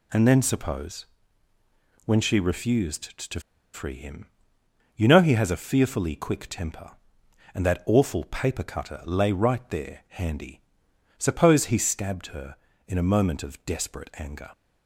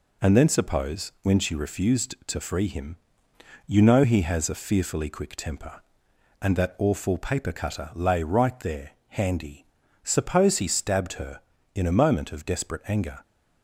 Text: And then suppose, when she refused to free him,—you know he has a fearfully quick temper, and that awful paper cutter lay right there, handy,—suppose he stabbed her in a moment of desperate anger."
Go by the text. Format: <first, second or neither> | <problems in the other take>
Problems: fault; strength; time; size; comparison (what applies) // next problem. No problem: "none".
second | pauses between "to" and "free"; slight; at 3.4 s; 0.33 s long